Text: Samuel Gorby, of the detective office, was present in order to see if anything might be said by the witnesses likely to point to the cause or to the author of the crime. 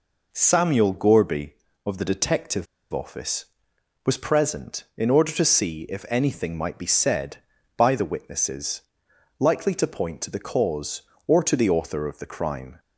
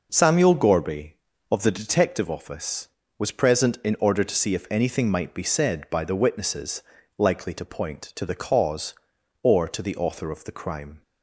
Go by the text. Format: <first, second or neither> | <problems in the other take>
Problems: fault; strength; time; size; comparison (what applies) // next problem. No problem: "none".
second | pauses between "detective" and "office"; slight; at 2.6 s; 0.27 s long // pauses between "witnesses" and "likely"; noticeable; at 8.8 s; 0.56 s long; also in the second